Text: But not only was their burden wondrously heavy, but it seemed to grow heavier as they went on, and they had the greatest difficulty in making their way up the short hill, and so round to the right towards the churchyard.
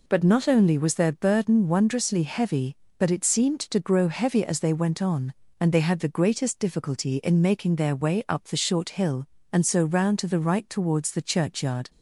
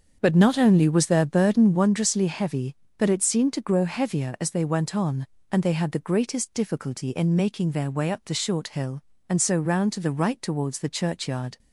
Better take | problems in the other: first | starts louder than the rest; until 1.9 s; 7 dB

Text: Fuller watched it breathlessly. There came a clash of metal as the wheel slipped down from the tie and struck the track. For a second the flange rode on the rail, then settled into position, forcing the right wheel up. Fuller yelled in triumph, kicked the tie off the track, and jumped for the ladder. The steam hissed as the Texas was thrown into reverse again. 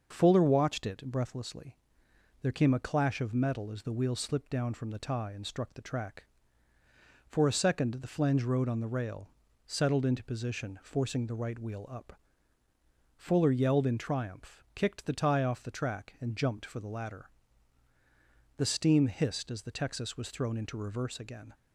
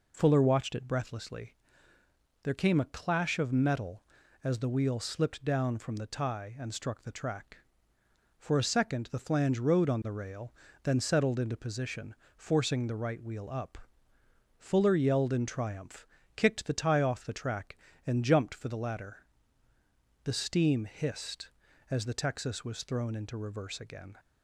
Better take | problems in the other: second | starts louder than the rest; until 1.1 s; 6.5 dB // skips "then"; at 9.4 s

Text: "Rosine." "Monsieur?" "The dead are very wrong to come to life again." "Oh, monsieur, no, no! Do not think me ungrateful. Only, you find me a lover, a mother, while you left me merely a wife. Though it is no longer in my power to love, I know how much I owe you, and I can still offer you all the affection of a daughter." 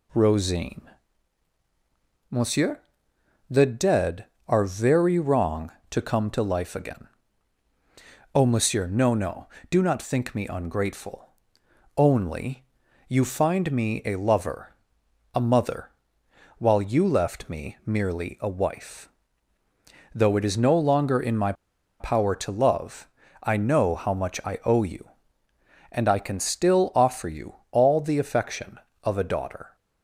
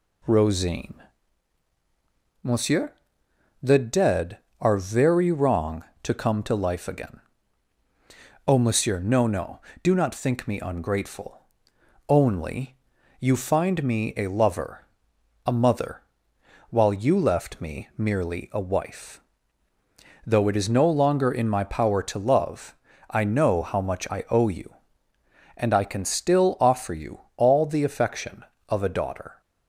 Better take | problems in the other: second | pauses between "my" and "power"; noticeable; at 21.5 s; 0.47 s long // pauses between "you" and "all"; slight; at 27.5 s; 0.18 s long; slight in the second

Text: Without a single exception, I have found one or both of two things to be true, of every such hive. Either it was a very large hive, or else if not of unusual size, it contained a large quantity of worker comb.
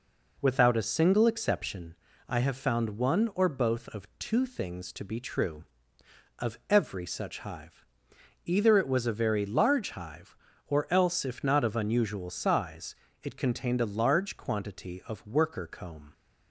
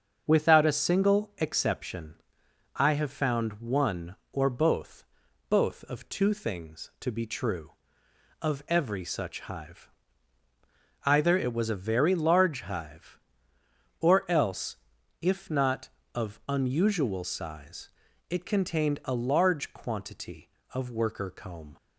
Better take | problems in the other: first | starts louder than the rest; until 1.2 s; 7 dB // says "both" twice; at 5.4 s // pauses between "else" and "if"; noticeable; at 14.7 s; 0.46 s long

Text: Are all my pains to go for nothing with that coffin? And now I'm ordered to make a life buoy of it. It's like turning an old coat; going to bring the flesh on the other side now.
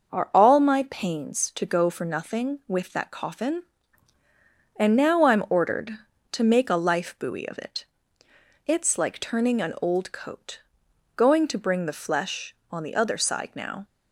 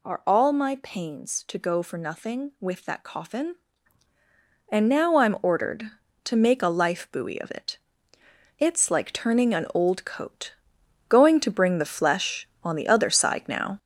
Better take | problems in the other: first | gets louder; noticeable; throughout; 5.5 dB

